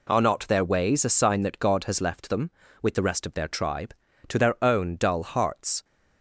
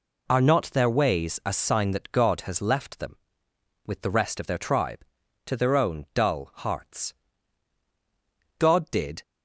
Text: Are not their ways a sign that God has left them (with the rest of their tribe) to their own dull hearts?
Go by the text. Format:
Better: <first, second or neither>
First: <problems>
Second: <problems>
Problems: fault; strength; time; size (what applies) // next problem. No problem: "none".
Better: first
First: none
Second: goes on to say "God did"; noticeable; from 8.5 s on; 0.64 s long